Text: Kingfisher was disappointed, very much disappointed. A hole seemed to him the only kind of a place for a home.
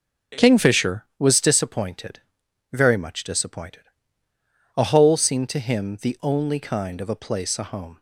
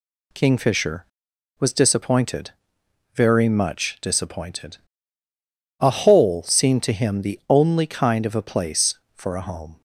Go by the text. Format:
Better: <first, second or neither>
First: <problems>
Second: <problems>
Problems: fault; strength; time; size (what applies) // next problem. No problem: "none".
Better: second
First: skips "for"; at 7.5 s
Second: none